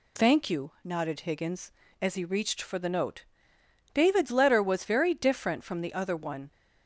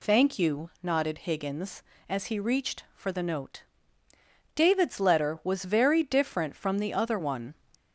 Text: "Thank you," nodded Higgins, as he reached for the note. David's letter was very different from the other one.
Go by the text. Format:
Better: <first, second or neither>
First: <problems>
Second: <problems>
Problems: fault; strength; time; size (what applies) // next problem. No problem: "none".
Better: first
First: none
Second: gets louder; slight; throughout; 2 dB